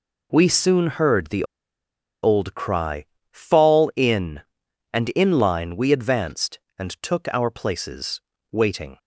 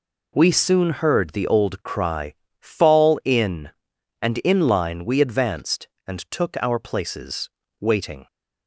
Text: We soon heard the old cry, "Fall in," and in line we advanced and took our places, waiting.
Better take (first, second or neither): second